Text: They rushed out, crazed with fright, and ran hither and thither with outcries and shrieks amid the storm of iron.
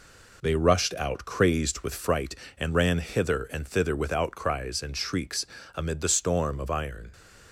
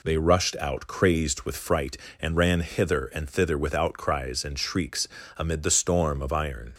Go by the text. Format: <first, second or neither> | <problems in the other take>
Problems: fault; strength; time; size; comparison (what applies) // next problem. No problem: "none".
second | gets quieter; noticeable; throughout; 6 dB // pauses between "shrieks" and "amid"; slight; at 5.4 s; 0.30 s long; slight in the second